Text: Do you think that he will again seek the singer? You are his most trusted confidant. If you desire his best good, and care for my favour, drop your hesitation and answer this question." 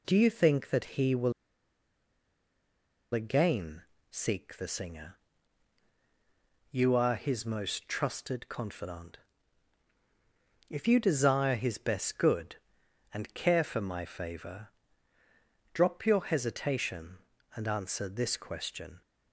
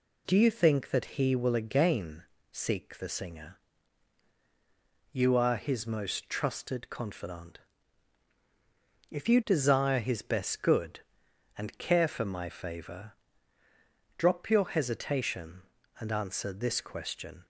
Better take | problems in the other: second | pauses between "will" and "again"; strong; at 1.3 s; 1.8 s long // pauses between "again" and "seek"; slight; at 3.8 s; 0.26 s long; slight in the second

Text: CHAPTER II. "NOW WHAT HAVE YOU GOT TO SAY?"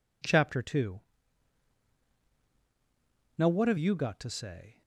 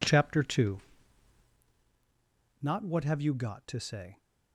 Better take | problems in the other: first | says "Not" for "NOW"; at 2.6 s

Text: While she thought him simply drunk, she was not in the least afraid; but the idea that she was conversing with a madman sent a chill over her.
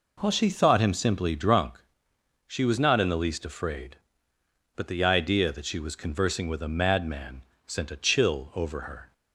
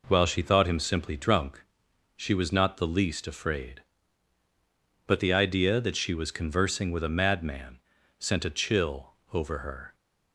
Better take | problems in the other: first | skips "in"; at 2.7 s // pauses between "madman" and "sent"; at 7.7 s; 0.40 s long; slight in the first // pauses between "chill" and "over"; slight; at 9.1 s; 0.18 s long

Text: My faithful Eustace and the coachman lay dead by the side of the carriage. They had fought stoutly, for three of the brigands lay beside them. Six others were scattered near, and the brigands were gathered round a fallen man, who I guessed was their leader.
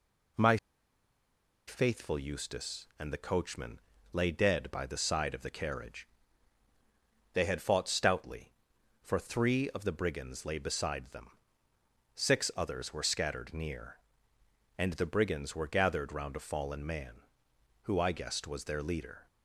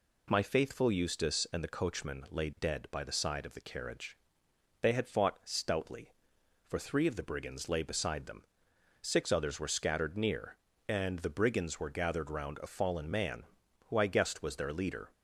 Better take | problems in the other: second | pauses between "My" and "faithful"; at 0.5 s; 1.1 s long // pauses between "coachman" and "lay"; slight; at 3.8 s; 0.32 s long

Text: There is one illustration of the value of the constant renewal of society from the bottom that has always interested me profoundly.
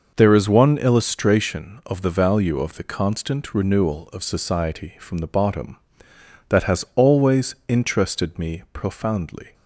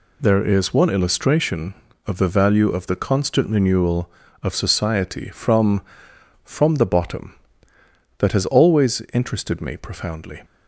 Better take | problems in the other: first | says "from" twice; at 6.4 s

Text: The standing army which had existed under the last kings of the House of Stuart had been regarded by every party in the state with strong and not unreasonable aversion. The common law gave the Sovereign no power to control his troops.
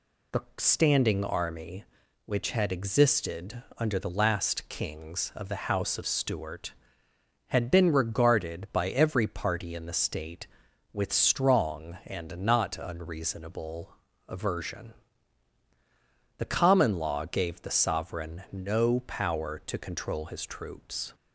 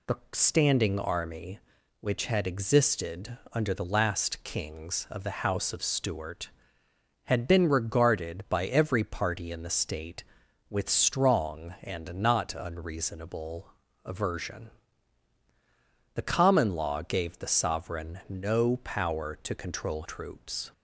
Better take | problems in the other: first | pauses between "unreasonable" and "aversion"; slight; at 13.7 s; 0.32 s long; slight in the first // skips "his"; at 20.0 s

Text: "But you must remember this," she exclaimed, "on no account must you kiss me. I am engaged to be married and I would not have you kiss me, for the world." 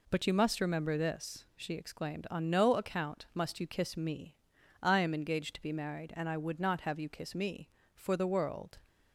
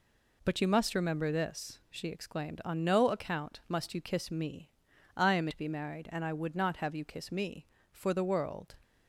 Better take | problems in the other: first | skips "engaged"; at 5.4 s

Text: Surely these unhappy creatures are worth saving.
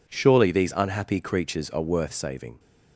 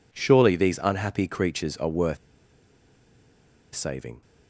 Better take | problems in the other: first | pauses between "worth" and "saving"; strong; at 2.1 s; 1.5 s long

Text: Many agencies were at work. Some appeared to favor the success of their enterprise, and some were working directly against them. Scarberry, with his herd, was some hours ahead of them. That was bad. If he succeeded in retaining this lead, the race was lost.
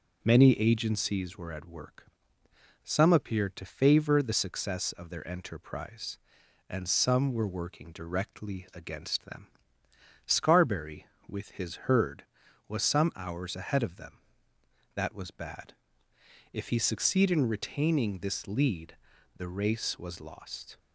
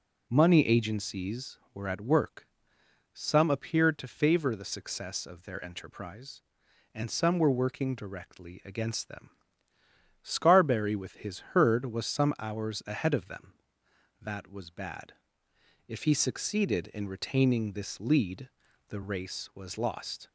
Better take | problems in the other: first | says "Money" for "Many"; at 0.2 s

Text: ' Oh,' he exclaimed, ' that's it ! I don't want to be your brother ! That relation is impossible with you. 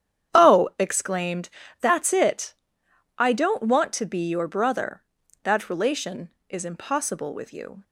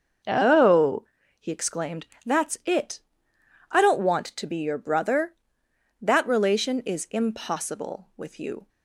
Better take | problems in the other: second | starts louder than the rest; strong; until 1.4 s; 9.5 dB; also in the second // skips "he"; at 0.7 s

